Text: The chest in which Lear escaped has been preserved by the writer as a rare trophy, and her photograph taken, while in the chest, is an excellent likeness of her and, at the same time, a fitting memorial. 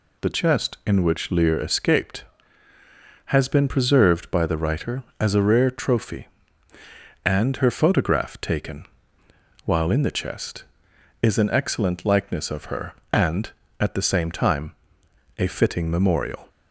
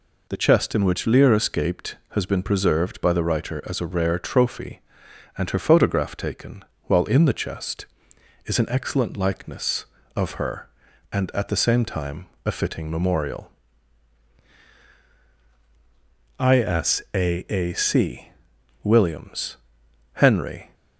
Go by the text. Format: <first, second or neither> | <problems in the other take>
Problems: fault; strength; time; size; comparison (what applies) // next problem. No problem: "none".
first | goes on to say "ISAAC WILLIAMS HENRY"; strong; from 16.3 s on; 4.3 s long